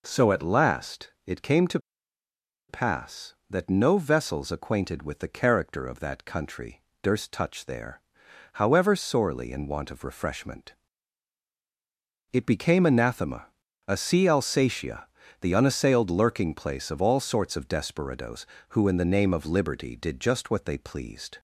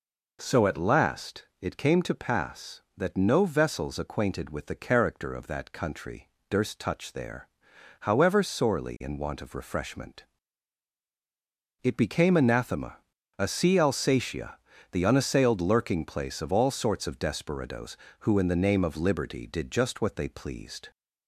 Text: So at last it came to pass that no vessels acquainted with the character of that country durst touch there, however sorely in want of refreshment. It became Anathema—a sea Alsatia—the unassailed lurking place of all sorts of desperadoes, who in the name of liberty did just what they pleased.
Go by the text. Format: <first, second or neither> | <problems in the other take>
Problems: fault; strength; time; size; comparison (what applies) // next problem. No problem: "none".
second | pauses between "last" and "it"; slight; at 1.0 s; 0.16 s long; slight in the second // pauses between "to" and "pass"; noticeable; at 1.7 s; 0.89 s long // pauses between "country" and "durst"; slight; at 6.8 s; 0.18 s long; slight in the second